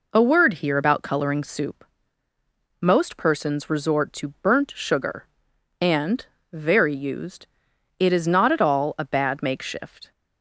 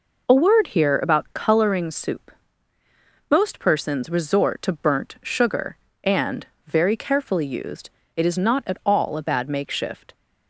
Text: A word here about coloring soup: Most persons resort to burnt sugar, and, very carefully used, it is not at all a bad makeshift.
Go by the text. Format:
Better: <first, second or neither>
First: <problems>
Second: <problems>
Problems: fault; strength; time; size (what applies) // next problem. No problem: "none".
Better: second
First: skips "carefully"; at 6.9 s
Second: none